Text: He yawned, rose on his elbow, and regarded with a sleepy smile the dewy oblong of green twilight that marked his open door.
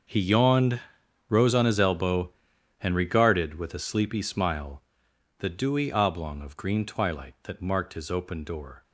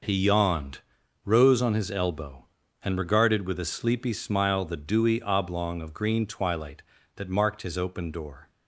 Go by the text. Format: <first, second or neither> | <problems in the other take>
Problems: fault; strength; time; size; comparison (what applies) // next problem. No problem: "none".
second | gets quieter; strong; throughout; 15 dB // pauses between "smile" and "the"; noticeable; at 4.8 s; 0.58 s long